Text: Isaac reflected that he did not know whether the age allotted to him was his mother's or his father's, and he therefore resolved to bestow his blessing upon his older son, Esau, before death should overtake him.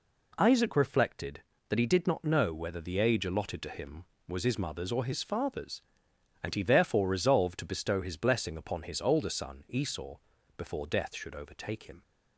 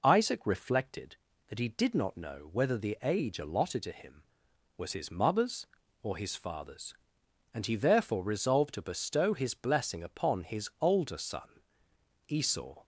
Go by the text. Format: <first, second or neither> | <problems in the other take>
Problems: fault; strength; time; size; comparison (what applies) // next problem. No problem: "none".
first | stops before "before death should overtake him"; at 12.8 s